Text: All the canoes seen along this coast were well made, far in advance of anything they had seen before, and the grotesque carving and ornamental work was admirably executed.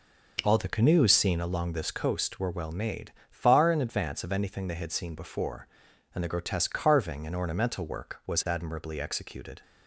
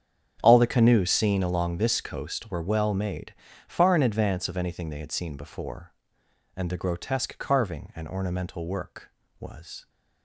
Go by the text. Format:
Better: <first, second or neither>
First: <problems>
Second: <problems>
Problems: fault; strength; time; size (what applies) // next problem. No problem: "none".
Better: first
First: none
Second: starts louder than the rest; strong; until 1.4 s; 7.5 dB // stops before "admirably executed"; at 9.8 s